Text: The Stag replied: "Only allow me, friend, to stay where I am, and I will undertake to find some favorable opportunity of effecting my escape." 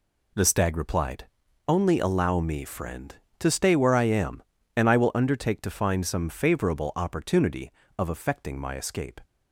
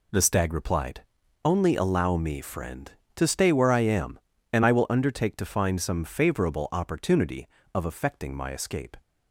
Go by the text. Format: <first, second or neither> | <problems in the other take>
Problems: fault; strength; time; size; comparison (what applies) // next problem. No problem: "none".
neither | none